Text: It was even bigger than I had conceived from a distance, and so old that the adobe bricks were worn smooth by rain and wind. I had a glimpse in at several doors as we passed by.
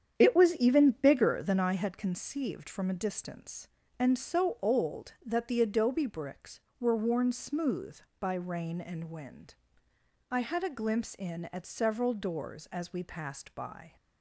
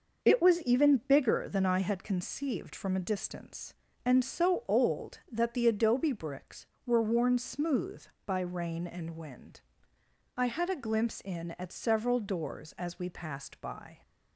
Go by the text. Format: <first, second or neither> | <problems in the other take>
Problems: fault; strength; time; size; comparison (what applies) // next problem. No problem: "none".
second | starts louder than the rest; strong; until 1.7 s; 8.5 dB